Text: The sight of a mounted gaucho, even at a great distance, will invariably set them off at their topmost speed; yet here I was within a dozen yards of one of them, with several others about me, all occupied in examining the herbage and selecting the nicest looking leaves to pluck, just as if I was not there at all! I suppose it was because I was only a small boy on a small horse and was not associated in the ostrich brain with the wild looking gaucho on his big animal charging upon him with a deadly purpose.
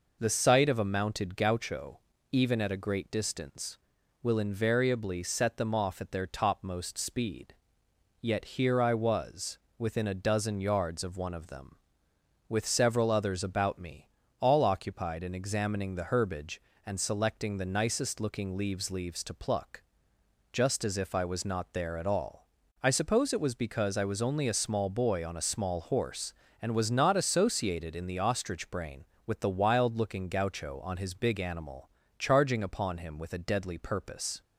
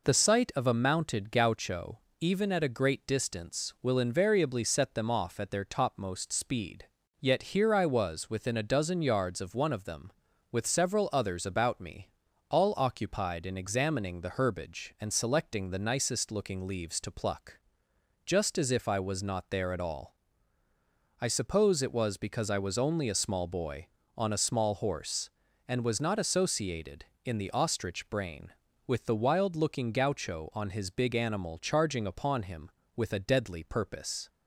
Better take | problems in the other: second | pauses between "was" and "within"; slight; at 9.5 s; 0.20 s long // says "leaves" twice; at 18.9 s // pauses between "animal" and "charging"; slight; at 31.8 s; 0.30 s long

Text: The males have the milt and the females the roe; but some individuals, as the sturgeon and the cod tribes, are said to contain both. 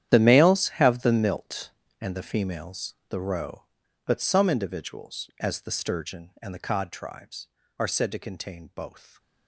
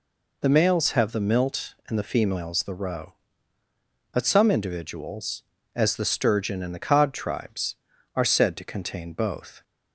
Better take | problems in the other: second | gets quieter; strong; throughout; 14.5 dB // pauses between "females" and "the"; slight; at 2.9 s; 0.16 s long

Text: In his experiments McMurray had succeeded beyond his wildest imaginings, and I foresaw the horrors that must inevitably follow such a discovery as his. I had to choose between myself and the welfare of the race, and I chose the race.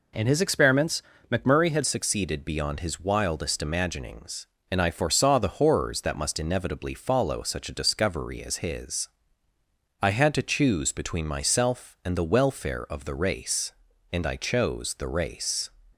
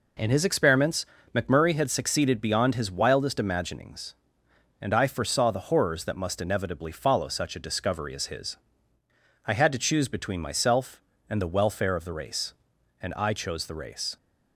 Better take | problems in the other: second | pauses between "experiments" and "McMurray"; slight; at 1.0 s; 0.28 s long; slight in the second // changes voice at "succeeded"; from 1.8 s on; 13.8 s long

